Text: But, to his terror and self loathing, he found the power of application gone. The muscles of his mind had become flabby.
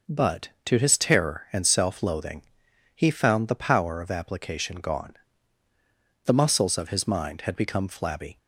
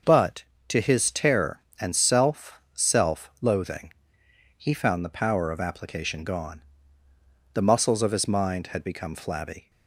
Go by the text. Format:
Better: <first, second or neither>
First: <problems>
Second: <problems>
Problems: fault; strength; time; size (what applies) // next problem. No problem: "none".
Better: first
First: none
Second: starts louder than the rest; noticeable; until 1.2 s; 6 dB // says "self" twice; at 2.7 s